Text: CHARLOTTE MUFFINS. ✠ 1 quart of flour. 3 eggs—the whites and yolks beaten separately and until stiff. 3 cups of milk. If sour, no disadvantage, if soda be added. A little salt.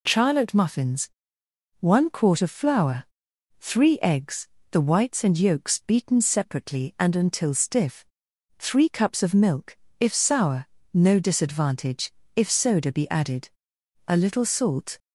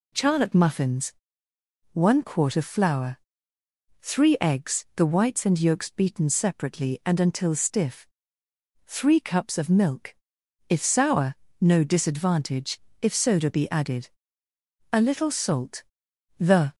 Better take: first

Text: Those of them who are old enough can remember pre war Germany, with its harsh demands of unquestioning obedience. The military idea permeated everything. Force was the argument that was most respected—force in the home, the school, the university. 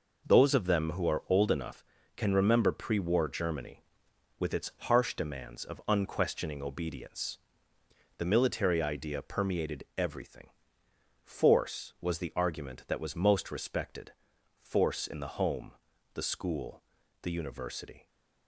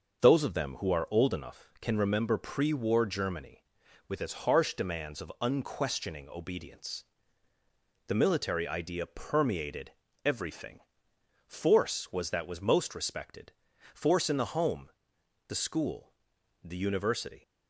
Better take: first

